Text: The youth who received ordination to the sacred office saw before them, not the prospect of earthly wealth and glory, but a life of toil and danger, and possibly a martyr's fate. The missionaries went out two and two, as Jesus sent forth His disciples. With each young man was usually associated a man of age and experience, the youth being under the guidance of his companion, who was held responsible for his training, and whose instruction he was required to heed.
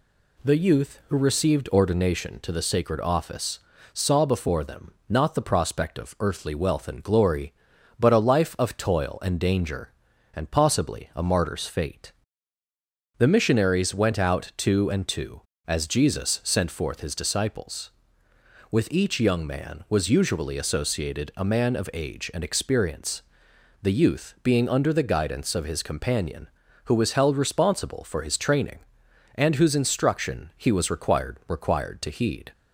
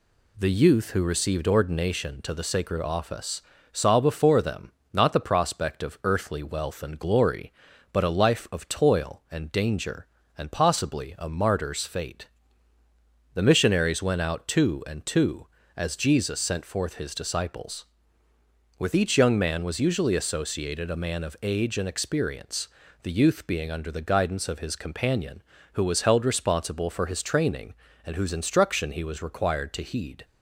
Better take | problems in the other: second | pauses between "office" and "saw"; slight; at 3.5 s; 0.34 s long; slight in the second // says "required" twice; at 31.4 s

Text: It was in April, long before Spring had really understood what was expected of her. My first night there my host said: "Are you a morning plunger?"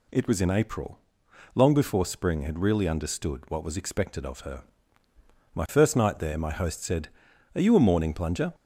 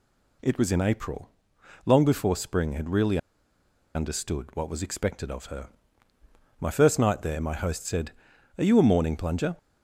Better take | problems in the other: first | pauses between "really" and "understood"; noticeable; at 3.1 s; 0.77 s long

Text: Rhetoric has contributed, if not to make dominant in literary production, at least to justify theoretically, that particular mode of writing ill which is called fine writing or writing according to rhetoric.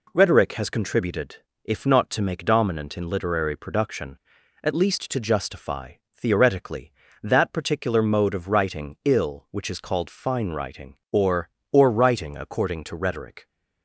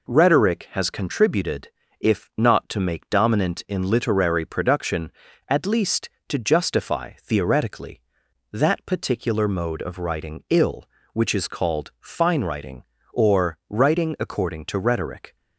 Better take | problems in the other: second | pauses between "justify" and "theoretically"; slight; at 5.9 s; 0.22 s long // says "or" twice; at 11.7 s

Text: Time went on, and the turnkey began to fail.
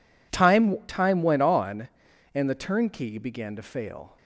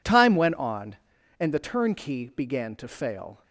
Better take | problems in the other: second | says "Time" twice; at 0.8 s

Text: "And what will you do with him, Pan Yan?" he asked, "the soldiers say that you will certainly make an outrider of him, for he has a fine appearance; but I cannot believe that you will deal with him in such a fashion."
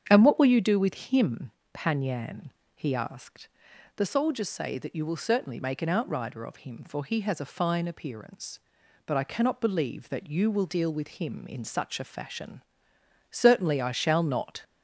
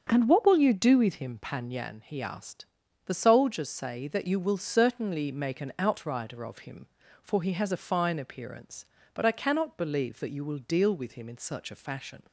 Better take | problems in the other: second | starts louder than the rest; strong; until 1.0 s; 8 dB; strong in the second // goes on to say "Certainly I shall not"; noticeable; from 13.3 s on; 1.3 s long

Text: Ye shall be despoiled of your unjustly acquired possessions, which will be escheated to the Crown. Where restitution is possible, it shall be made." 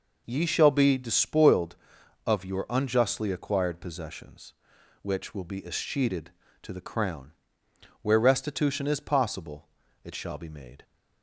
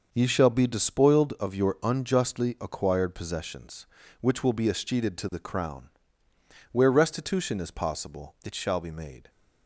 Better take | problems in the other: neither | none

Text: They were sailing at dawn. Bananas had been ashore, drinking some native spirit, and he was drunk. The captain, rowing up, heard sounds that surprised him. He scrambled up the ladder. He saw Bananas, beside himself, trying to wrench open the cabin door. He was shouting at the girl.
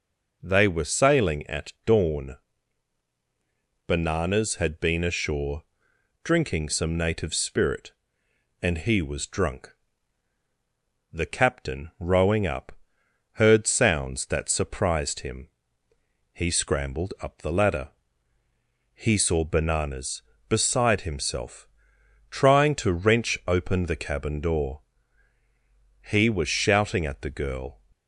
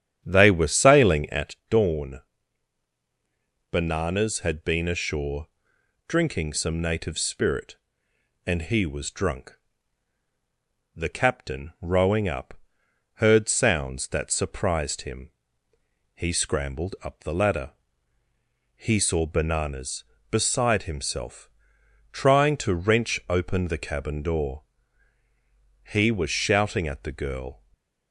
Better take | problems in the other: first | starts louder than the rest; strong; until 1.5 s; 9 dB // stays silent after the last word; slight; from 27.5 s on; 0.6 s long

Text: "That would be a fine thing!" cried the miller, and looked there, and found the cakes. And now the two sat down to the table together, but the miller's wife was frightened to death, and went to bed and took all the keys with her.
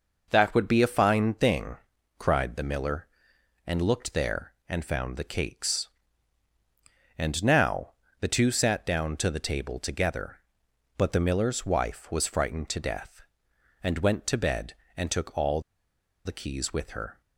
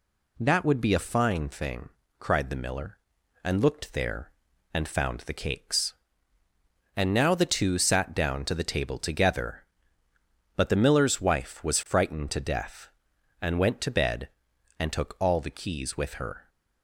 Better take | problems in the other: second | pauses between "now" and "the"; slight; at 7.9 s; 0.26 s long // pauses between "all" and "the"; noticeable; at 15.6 s; 0.63 s long

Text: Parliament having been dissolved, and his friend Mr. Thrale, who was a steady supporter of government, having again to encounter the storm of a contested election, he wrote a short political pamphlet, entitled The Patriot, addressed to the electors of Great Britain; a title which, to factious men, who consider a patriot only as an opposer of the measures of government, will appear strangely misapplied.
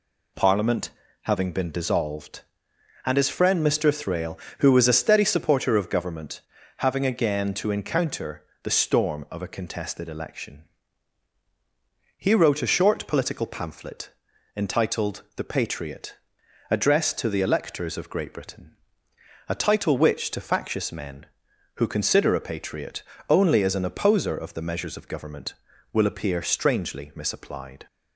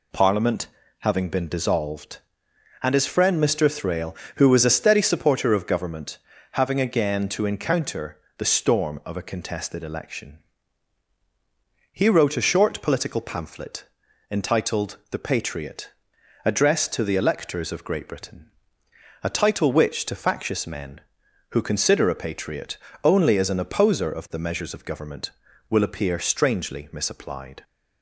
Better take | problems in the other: neither | pauses between "Parliament" and "having"; slight; the same in both // pauses between "encounter" and "the"; slight; the same in both // pauses between "patriot" and "only"; slight; the same in both

